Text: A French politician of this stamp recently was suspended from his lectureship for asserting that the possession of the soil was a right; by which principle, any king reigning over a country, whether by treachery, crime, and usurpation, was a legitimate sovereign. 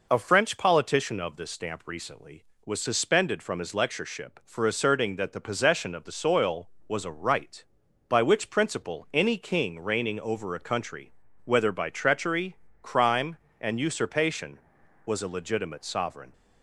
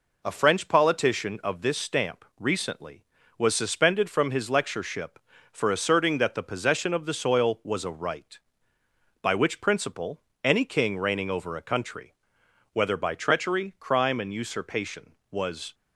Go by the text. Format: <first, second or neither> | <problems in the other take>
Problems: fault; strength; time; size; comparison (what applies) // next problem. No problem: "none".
first | stops before "a legitimate sovereign"; at 15.7 s